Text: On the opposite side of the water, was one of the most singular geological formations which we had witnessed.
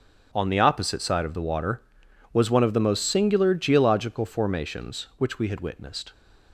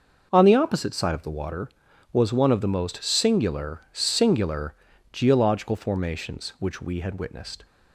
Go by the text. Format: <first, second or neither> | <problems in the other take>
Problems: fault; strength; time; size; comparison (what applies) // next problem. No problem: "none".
first | starts louder than the rest; noticeable; until 1.3 s; 6 dB; also in the first // says "singular" twice; at 3.9 s